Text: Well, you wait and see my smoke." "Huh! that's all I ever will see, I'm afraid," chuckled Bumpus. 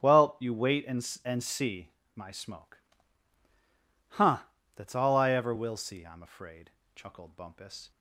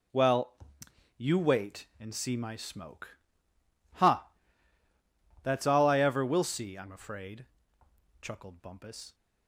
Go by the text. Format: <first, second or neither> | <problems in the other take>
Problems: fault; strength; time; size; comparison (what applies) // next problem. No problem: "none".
second | starts louder than the rest; strong; until 1.0 s; 10 dB // says "and" twice; at 1.2 s // pauses between "see" and "my"; slight; at 1.9 s; 0.26 s long